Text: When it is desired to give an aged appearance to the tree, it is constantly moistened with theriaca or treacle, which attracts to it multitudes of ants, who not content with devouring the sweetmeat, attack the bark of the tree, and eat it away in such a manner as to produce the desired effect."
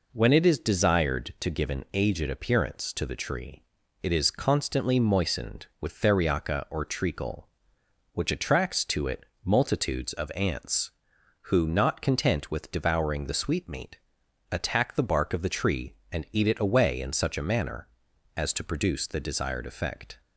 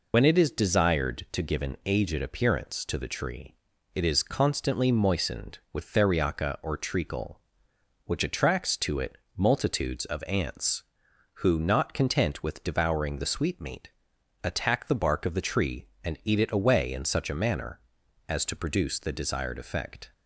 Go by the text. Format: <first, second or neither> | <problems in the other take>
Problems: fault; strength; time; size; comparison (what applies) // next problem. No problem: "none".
first | loses the start of "When"; at 0.1 s; 100 ms // pauses between "it" and "multitudes"; slight; at 9.1 s; 0.20 s long; slight in the first